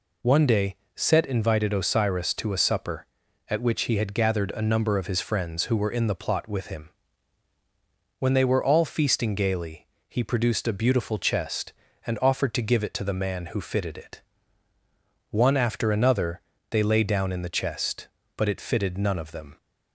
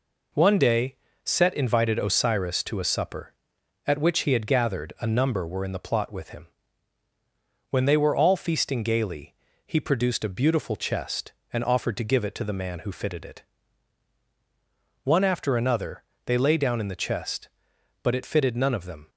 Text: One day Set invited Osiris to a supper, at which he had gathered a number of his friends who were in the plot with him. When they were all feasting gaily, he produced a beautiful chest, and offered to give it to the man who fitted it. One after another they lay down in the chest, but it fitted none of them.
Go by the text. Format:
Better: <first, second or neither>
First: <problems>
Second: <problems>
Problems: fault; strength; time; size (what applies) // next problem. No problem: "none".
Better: first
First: pauses between "day" and "Set"; slight; at 0.7 s; 0.20 s long // pauses between "another" and "they"; slight; at 16.4 s; 0.28 s long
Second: pauses between "day" and "Set"; slight; at 0.9 s; 0.28 s long // skips "of his friends who"; at 5.4 s // pauses between "another" and "they"; slight; at 16.0 s; 0.24 s long